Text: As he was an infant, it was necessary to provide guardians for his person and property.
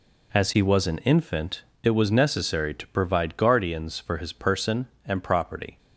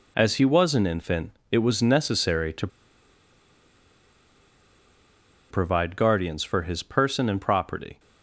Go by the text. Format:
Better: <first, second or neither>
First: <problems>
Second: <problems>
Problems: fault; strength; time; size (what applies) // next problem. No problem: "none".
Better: first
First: none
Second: pauses between "to" and "provide"; strong; at 2.6 s; 2.8 s long